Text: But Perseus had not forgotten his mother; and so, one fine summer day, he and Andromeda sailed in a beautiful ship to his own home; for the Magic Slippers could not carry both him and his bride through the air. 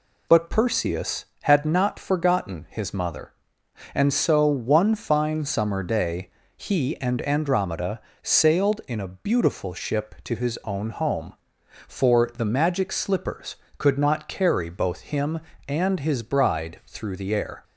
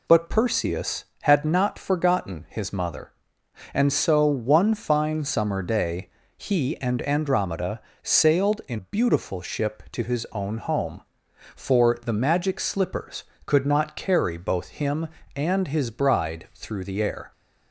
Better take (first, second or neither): first